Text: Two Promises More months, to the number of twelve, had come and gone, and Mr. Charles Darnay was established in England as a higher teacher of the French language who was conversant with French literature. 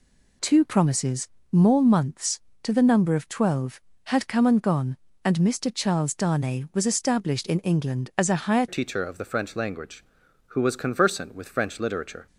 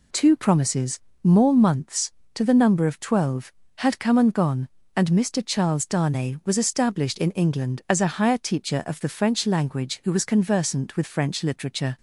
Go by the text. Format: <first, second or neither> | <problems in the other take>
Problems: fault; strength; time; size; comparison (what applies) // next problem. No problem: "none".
second | pauses between "Promises" and "More"; slight; at 1.2 s; 0.24 s long; slight in the second // changes voice at "teacher"; from 8.6 s on; 3.6 s long